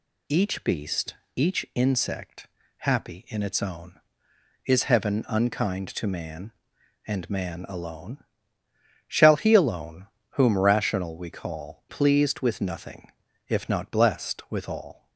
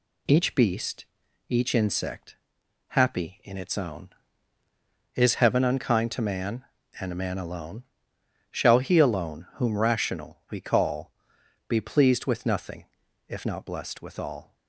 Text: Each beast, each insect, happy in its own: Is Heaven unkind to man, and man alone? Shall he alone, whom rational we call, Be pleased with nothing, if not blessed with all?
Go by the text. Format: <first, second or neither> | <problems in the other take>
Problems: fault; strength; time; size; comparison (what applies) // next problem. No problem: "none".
second | skips "Be"; at 11.8 s